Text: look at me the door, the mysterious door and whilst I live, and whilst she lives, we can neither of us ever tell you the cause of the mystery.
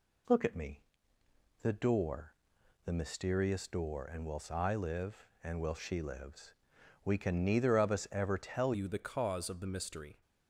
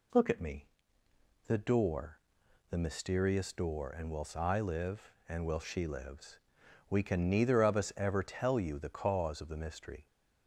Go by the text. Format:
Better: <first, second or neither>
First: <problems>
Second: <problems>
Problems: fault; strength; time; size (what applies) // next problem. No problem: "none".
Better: second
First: pauses between "me" and "the"; noticeable; at 0.8 s; 0.80 s long // changes voice at "you"; from 8.7 s on; 1.5 s long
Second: pauses between "me" and "the"; noticeable; at 0.6 s; 0.80 s long